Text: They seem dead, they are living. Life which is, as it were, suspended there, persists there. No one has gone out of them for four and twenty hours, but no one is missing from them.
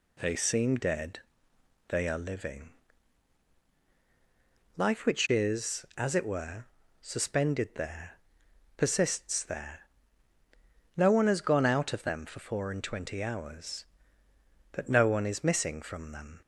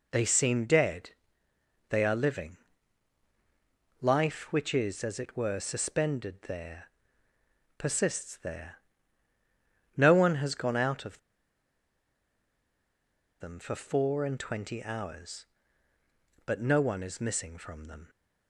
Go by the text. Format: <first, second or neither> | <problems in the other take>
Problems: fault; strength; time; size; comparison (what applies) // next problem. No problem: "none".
first | pauses between "of" and "them"; strong; at 11.1 s; 2.2 s long